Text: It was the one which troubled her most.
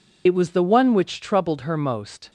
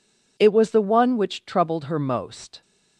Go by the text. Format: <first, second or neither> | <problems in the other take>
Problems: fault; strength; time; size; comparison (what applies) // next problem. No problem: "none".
second | loses the start of "It"; at 0.2 s; 50 ms